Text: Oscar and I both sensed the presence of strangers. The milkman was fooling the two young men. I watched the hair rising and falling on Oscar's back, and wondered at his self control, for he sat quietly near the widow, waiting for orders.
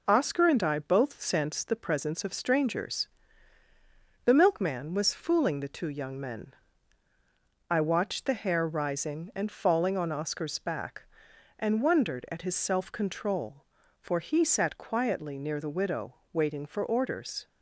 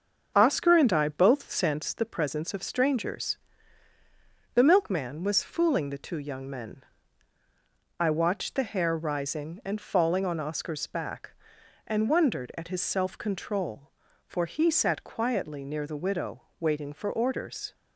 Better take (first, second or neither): first